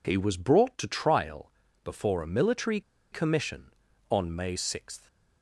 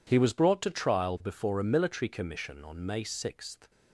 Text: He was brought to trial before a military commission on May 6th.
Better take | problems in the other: second | pauses between "trial" and "before"; slight; at 1.4 s; 0.34 s long // pauses between "military" and "commission"; slight; at 2.7 s; 0.32 s long

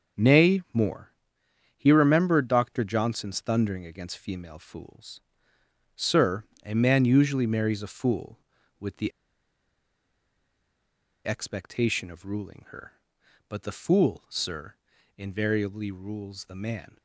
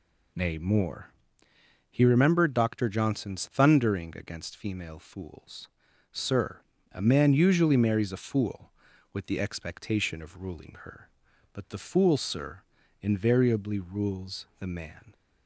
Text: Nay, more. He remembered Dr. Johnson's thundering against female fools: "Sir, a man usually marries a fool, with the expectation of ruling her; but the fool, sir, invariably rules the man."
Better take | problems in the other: second | starts louder than the rest; until 1.9 s; 6.5 dB // pauses between "the" and "expectation"; strong; at 9.1 s; 2.1 s long

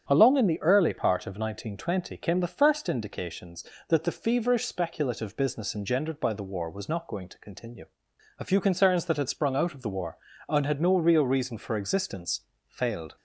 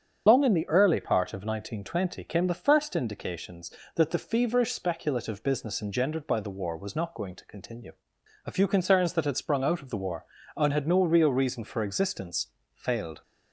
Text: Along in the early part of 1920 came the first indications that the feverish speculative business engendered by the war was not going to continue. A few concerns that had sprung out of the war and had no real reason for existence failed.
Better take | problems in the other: first | loses the start of "Along"; at 0.2 s; 120 ms // starts louder than the rest; strong; until 1.2 s; 7.5 dB; strong in the first // pauses between "existence" and "failed"; slight; at 12.4 s; 0.26 s long; slight in the first

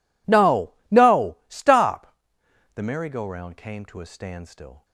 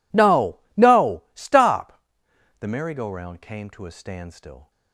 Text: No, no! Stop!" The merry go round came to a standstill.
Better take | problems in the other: neither | none

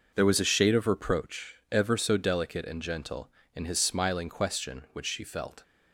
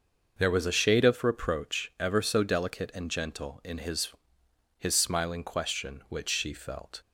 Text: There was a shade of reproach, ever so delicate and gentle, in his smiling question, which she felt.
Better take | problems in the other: first | starts louder than the rest; until 1.3 s; 6 dB // says "his" twice; at 4.7 s

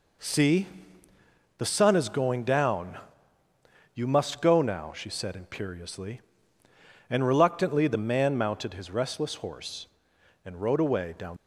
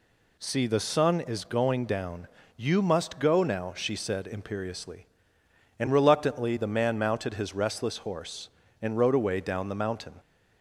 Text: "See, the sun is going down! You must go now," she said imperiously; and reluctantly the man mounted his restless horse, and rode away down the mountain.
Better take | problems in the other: second | stops before "the mountain"; at 11.3 s

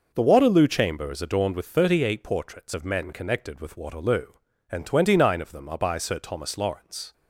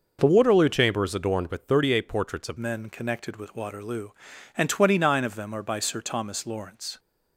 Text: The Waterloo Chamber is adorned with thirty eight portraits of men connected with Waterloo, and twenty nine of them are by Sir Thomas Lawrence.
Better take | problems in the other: first | changes voice at "men"; from 2.5 s on; 4.4 s long

